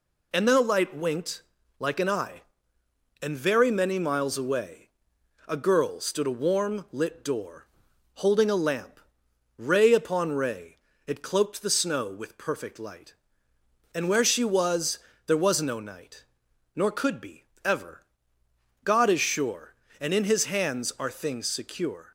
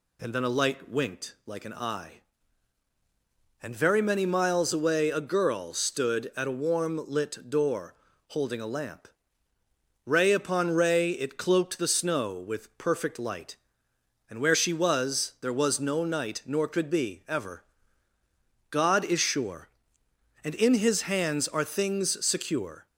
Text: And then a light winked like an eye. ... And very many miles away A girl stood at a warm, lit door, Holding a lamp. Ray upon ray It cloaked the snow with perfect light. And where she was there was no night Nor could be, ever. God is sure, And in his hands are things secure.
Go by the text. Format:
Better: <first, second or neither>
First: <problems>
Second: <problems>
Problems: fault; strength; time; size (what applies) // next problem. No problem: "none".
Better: second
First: pauses between "winked" and "like"; slight; at 1.4 s; 0.36 s long // pauses between "away" and "A"; noticeable; at 4.8 s; 0.58 s long // skips "at"; at 6.2 s // pauses between "ray" and "It"; slight; at 10.7 s; 0.30 s long // pauses between "was" and "there"; slight; at 14.9 s; 0.26 s long // pauses between "night" and "Nor"; noticeable; at 16.2 s; 0.50 s long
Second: none